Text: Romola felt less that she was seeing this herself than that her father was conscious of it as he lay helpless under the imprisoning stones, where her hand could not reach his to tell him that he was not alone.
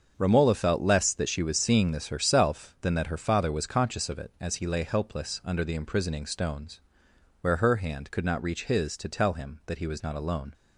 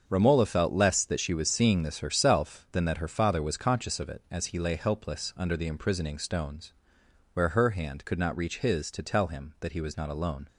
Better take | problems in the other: neither | starts louder than the rest; the same in both

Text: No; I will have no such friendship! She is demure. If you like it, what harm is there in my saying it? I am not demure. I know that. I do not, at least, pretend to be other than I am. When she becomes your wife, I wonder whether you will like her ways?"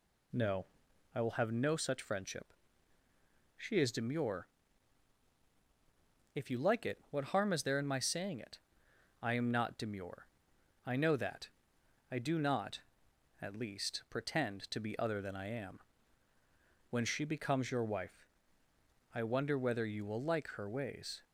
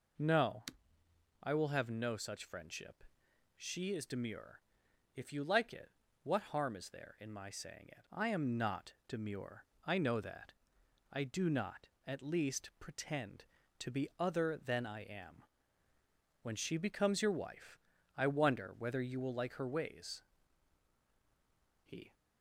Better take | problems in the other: first | goes on to say "He"; slight; from 21.8 s on; 0.30 s long

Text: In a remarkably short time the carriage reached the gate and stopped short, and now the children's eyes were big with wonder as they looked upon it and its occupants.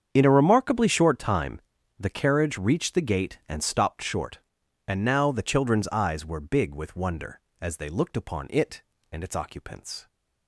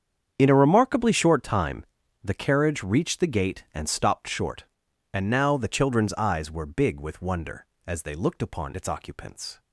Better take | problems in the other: first | starts louder than the rest; strong; until 1.3 s; 8 dB; strong in the first // pauses between "time" and "the"; slight; at 1.8 s; 0.36 s long; slight in the first // skips "it and"; at 8.7 s

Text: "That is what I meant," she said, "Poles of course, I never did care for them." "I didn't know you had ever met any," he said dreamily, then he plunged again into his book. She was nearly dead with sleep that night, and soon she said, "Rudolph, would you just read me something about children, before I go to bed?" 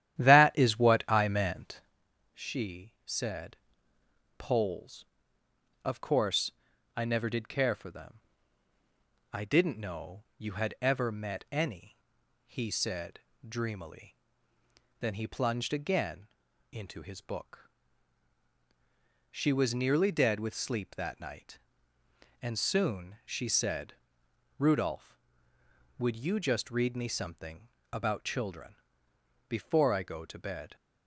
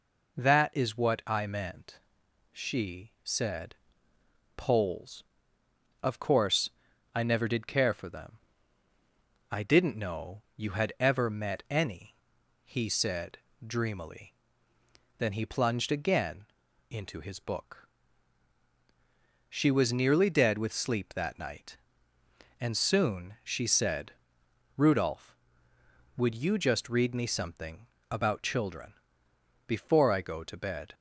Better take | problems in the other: second | starts louder than the rest; strong; until 1.9 s; 11.5 dB // pauses between "said" and "dreamily"; slight; at 13.2 s; 0.26 s long; slight in the second // pauses between "again" and "into"; noticeable; at 16.2 s; 0.46 s long; noticeable in the second // pauses between "something" and "about"; slight; at 27.6 s; 0.24 s long; slight in the second

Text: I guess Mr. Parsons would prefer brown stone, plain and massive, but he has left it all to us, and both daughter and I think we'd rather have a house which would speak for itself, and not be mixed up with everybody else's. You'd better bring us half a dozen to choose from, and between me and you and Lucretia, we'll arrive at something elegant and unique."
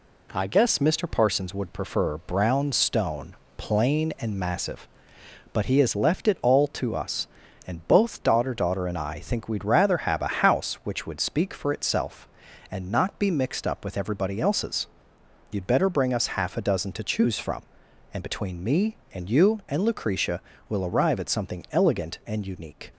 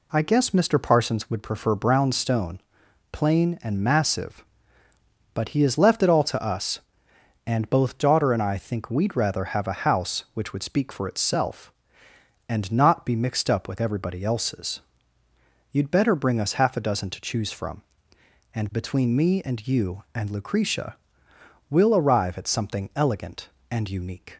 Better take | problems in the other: second | says "daughter" twice; at 8.5 s

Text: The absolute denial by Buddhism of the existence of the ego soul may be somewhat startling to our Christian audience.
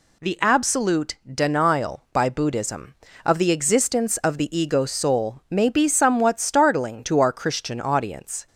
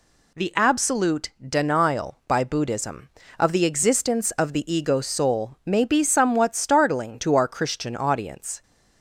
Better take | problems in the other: neither | none

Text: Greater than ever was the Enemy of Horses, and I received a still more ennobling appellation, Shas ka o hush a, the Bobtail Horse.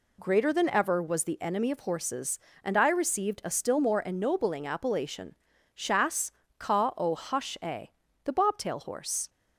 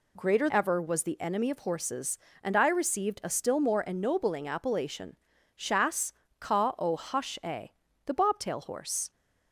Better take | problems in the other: first | skips "than"; at 0.4 s // pauses between "Shas" and "ka"; slight; at 6.1 s; 0.26 s long; slight in the first

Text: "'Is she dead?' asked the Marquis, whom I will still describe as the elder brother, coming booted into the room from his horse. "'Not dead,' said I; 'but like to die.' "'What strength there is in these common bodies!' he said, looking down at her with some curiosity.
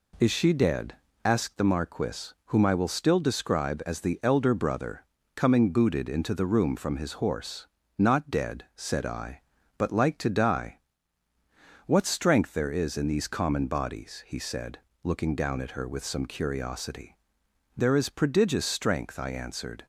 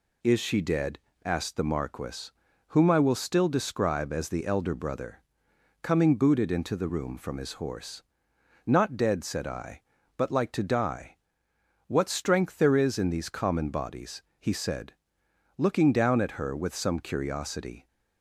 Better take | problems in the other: second | goes on to say "There is prodigious strength I answered"; strong; from 17.7 s on; 2.1 s long

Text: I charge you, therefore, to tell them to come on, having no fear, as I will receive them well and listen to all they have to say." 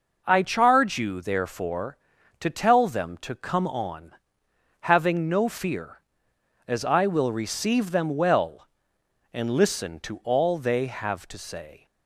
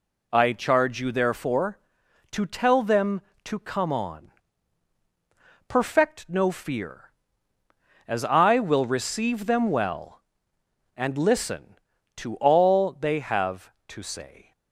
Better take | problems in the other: first | says "perfect" for "having"; at 5.6 s

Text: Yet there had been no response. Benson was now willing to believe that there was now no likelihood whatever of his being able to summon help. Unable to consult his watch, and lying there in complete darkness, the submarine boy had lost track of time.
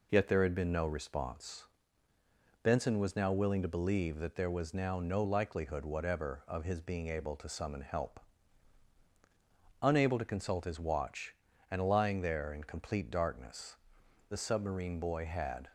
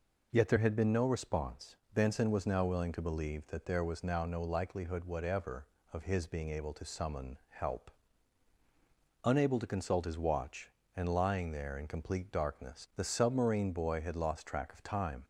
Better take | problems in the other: second | stops before "lost track of time"; at 15.6 s

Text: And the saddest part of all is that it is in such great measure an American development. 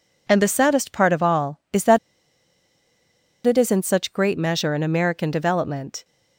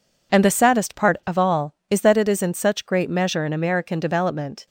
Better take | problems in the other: second | pauses between "that" and "it"; strong; at 1.9 s; 1.4 s long

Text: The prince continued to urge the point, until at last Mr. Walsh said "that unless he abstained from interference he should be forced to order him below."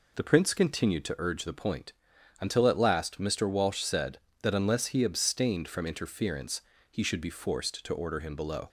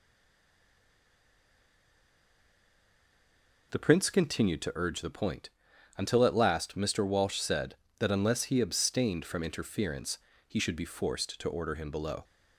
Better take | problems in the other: first | stays silent before the first word; strong; until 3.7 s; 3.7 s long // pauses between "interference" and "he"; slight; at 10.1 s; 0.30 s long; slight in the first

